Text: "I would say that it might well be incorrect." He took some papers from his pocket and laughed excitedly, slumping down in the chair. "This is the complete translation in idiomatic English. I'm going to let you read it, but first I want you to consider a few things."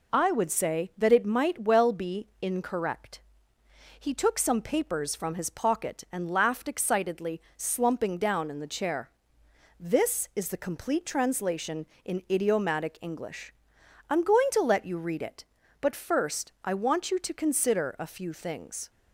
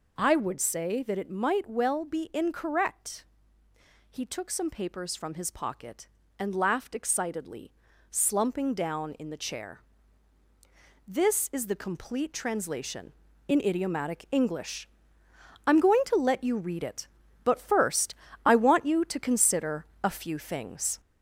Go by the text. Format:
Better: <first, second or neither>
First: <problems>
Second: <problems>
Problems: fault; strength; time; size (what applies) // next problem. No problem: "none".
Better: first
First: none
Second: gets louder; throughout; 4 dB // pauses between "first" and "I"; slight; at 18.1 s; 0.32 s long // pauses between "consider" and "a"; slight; at 19.8 s; 0.16 s long